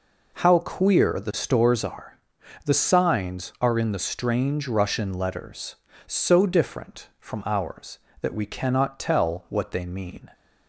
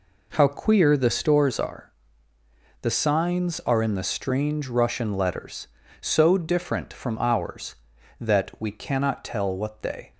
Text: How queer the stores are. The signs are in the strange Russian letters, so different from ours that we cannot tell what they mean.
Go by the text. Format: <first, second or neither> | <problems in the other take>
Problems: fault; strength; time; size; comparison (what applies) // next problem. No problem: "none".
first | stops before "mean"; at 10.1 s